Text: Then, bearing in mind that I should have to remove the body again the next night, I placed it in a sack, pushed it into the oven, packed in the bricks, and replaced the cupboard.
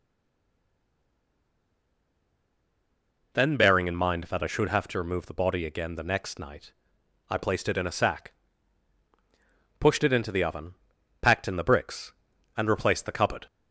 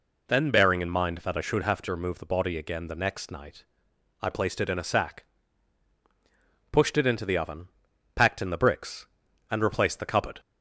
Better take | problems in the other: second | stays silent before the first word; strong; until 3.3 s; 3.3 s long

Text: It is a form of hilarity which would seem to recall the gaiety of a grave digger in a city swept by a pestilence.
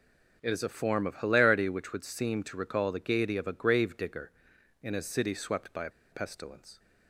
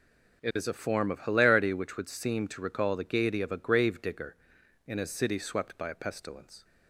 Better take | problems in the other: second | pauses between "a" and "pestilence"; slight; at 5.8 s; 0.21 s long

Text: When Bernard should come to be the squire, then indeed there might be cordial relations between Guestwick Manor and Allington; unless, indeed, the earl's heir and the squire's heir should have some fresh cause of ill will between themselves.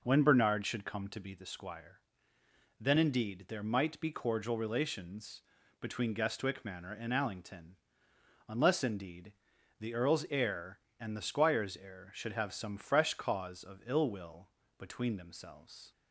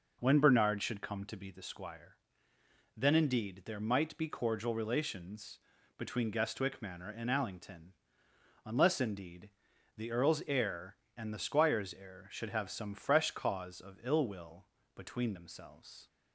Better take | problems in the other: neither | pauses between "relations" and "between"; slight; the same in both // pauses between "will" and "between"; slight; the same in both

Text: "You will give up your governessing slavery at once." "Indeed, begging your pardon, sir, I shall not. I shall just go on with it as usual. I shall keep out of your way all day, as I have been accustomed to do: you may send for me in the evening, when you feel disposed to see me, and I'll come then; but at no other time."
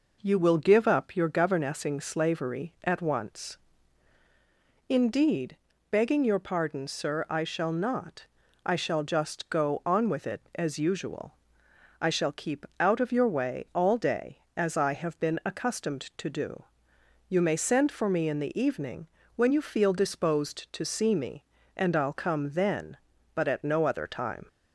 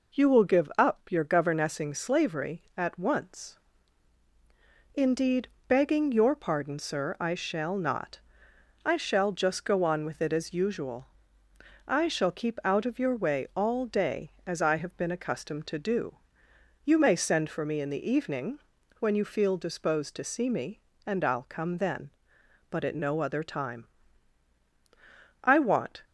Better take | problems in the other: first | goes on to say "I want"; from 25.4 s on; 0.60 s long

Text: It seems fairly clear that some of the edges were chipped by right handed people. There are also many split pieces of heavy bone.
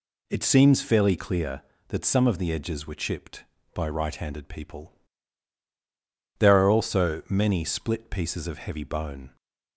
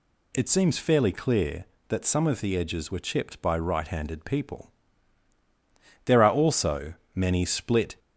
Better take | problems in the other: first | pauses between "also" and "many"; slight; at 6.9 s; 0.20 s long // stops before "pieces of heavy bone"; at 7.9 s

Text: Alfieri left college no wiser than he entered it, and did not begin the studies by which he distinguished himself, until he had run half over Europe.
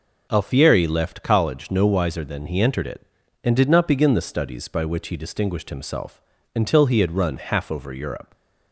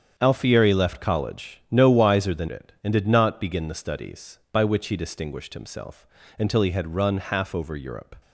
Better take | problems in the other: first | starts louder than the rest; strong; until 1.1 s; 7.5 dB // skips "he entered"; at 2.4 s

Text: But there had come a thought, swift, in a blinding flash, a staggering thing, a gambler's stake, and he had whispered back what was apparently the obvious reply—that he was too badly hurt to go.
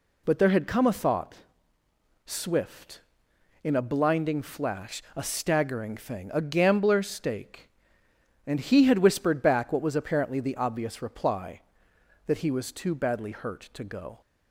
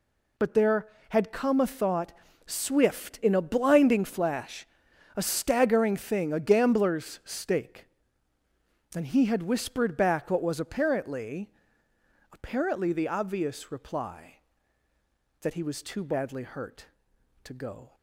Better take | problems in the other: first | says "apparently" twice; at 12.3 s

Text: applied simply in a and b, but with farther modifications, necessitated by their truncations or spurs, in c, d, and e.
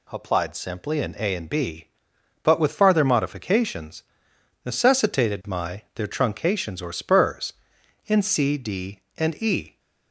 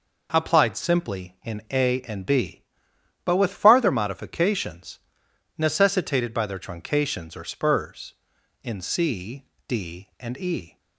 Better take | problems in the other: second | says "my" for "by"; at 5.4 s

